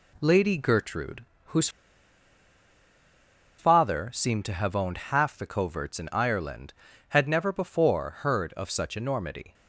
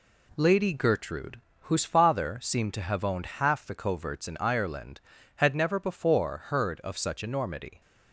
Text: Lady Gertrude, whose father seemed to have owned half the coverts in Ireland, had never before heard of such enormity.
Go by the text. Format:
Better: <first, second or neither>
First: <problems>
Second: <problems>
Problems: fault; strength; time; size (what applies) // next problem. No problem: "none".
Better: second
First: pauses between "whose" and "father"; strong; at 1.6 s; 1.9 s long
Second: none